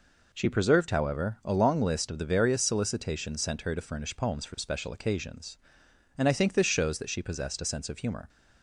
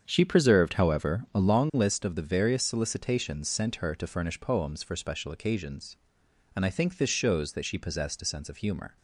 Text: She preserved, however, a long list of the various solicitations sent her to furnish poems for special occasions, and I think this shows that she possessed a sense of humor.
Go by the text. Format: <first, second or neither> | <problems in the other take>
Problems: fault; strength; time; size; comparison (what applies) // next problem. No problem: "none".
first | starts louder than the rest; strong; until 1.6 s; 7.5 dB